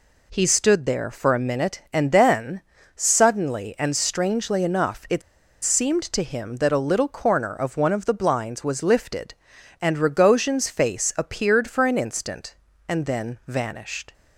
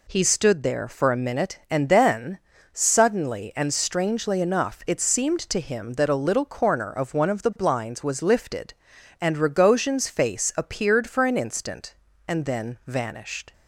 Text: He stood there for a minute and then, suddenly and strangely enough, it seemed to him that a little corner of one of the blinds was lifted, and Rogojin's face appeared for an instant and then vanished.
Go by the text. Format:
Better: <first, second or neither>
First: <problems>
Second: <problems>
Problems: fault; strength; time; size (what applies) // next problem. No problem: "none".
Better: second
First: pauses between "it" and "seemed"; at 5.2 s; 0.43 s long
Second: none